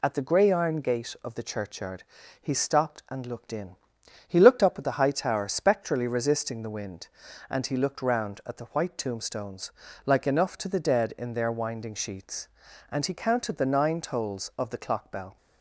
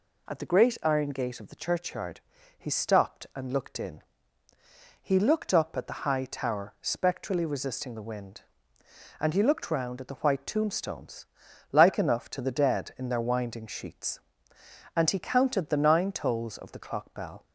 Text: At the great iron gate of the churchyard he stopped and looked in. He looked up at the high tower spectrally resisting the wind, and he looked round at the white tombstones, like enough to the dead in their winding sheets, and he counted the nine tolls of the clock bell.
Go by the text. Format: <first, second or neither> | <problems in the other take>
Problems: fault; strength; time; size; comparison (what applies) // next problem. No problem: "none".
second | says "grey" for "great"; at 0.2 s // pauses between "churchyard" and "he"; at 2.0 s; 0.38 s long; slight in the second